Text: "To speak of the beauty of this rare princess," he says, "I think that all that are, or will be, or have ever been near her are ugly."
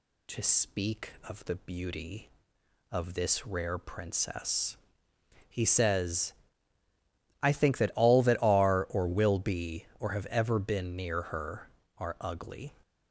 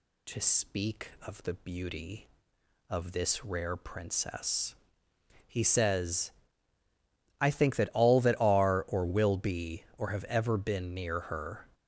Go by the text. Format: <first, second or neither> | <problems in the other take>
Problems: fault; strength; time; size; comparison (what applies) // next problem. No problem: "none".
first | stops before "are ugly"; at 11.7 s